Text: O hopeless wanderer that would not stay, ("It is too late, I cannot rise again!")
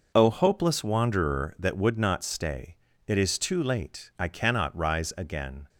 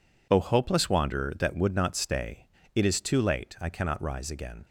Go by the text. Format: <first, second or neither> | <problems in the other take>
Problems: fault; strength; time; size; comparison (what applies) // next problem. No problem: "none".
neither | none